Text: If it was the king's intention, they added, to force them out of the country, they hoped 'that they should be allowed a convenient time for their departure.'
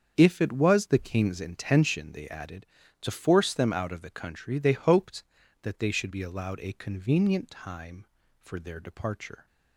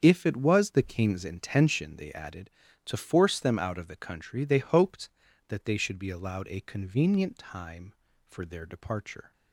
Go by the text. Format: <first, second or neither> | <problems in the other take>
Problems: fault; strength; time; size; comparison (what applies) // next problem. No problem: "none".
neither | starts louder than the rest; strong; the same in both